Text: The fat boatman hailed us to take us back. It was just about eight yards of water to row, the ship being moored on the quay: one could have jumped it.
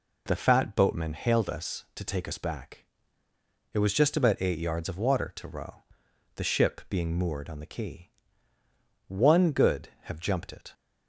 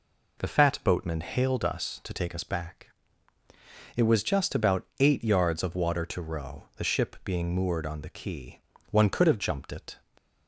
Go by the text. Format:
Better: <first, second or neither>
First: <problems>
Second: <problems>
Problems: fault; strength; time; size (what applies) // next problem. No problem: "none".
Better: second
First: says "good" for "could"; at 9.5 s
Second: none